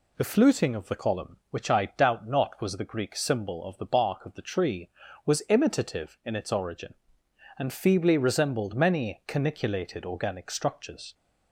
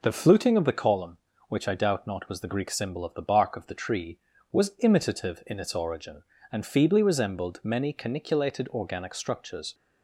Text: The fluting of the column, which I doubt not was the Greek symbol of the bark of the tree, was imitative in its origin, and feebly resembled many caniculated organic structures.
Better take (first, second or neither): neither